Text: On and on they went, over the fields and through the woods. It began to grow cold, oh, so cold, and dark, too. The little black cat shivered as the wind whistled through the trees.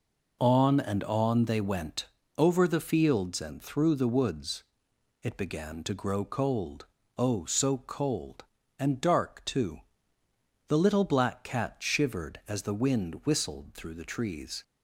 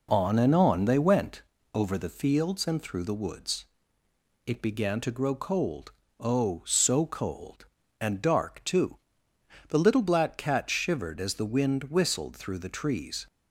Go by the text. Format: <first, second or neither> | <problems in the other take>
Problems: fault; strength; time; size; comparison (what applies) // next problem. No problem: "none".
neither | none